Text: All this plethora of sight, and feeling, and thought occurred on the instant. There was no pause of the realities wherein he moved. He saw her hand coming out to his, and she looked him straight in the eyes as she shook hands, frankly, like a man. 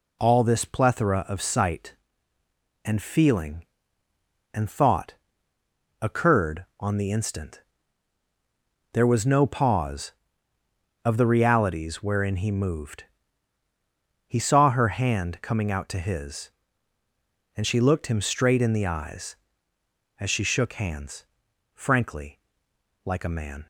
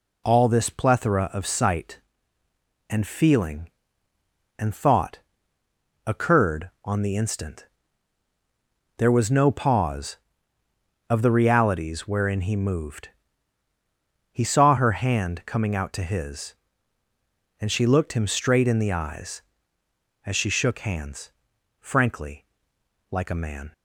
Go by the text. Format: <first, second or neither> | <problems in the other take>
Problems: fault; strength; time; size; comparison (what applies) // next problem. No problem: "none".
neither | pauses between "thought" and "occurred"; noticeable; the same in both